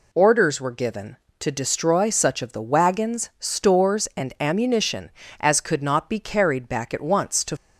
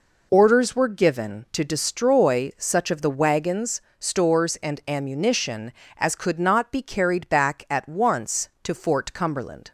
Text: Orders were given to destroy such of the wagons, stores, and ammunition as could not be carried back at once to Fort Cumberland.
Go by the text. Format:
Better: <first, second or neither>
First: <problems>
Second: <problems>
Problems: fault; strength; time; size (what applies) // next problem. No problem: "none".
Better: second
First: stops before "Fort Cumberland"; at 7.5 s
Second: none